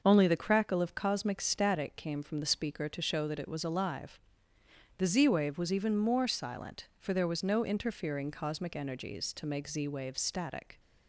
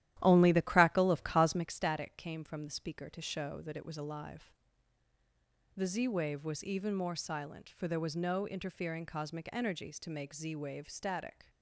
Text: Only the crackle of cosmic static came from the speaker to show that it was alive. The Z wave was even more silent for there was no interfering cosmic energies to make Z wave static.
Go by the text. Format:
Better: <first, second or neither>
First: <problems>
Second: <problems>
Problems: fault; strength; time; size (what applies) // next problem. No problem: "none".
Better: first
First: none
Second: starts louder than the rest; strong; until 1.8 s; 13 dB